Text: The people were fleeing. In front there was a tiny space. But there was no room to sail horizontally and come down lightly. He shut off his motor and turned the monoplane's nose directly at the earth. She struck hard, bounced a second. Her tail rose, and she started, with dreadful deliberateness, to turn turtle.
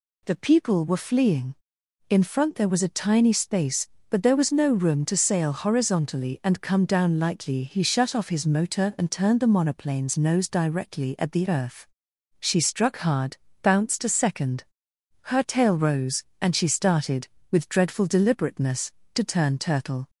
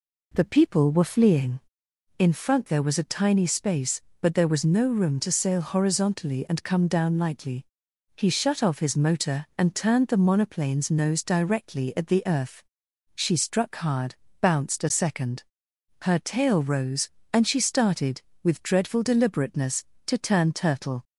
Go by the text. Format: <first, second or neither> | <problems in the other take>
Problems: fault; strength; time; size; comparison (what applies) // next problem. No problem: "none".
first | starts louder than the rest; until 2.0 s; 3.5 dB